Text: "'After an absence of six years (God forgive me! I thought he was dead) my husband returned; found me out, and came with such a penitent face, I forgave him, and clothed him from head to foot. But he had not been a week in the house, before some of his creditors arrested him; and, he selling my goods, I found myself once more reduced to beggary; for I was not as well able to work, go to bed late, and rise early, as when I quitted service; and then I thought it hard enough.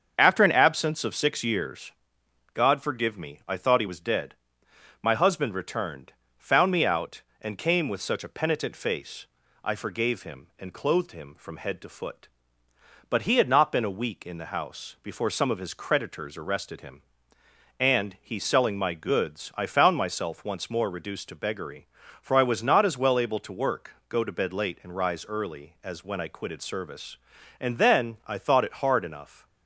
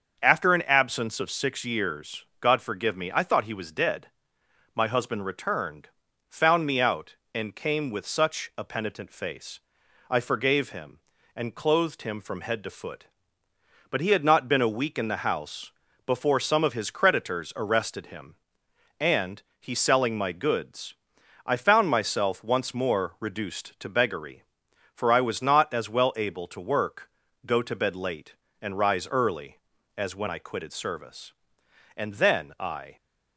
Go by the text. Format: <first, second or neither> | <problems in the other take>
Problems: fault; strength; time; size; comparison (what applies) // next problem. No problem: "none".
first | starts louder than the rest; until 1.2 s; 6.5 dB; also in the first // stops before "thought it hard enough"; at 32.9 s